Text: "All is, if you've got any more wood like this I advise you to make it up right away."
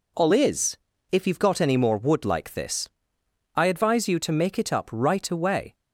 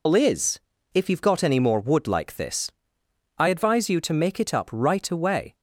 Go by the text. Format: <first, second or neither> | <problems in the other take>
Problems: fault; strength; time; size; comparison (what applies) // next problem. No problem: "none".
first | loses the start of "All"; at 0.0 s; 85 ms // pauses between "this" and "I"; noticeable; at 2.6 s; 0.68 s long; noticeable in the first